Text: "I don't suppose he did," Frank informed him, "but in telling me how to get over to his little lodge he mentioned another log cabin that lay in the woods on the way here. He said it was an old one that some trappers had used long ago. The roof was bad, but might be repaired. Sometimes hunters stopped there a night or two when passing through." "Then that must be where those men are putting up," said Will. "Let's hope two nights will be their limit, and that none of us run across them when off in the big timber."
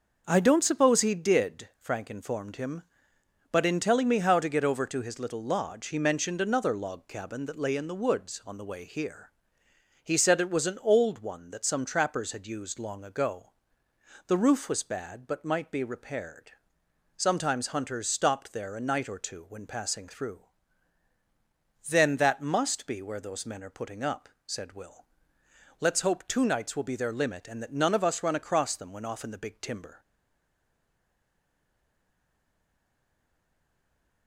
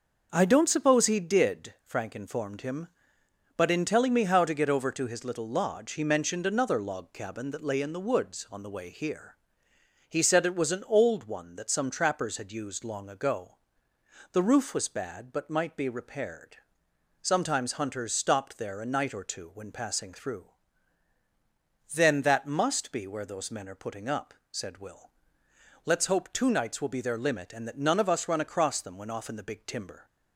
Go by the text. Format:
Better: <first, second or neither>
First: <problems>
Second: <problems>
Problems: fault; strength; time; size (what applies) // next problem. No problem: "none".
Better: second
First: starts louder than the rest; until 1.2 s; 6 dB // stays silent after the last word; strong; from 30.0 s on; 4.2 s long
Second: starts louder than the rest; until 1.3 s; 6 dB